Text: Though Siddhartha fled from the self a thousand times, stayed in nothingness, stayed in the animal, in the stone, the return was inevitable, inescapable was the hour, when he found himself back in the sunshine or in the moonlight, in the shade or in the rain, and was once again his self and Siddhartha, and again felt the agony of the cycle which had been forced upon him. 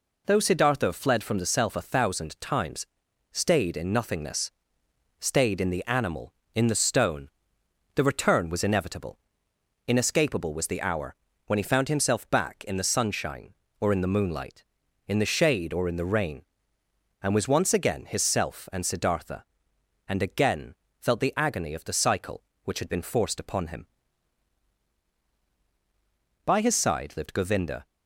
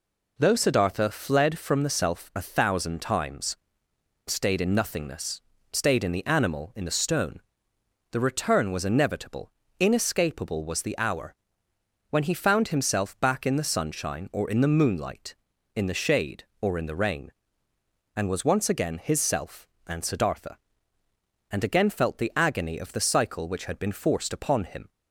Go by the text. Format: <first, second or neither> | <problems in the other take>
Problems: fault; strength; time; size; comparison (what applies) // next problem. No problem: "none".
second | pauses between "again" and "felt"; slight; at 20.7 s; 0.24 s long // goes on to say "By his side lived Govinda"; from 26.4 s on; 1.4 s long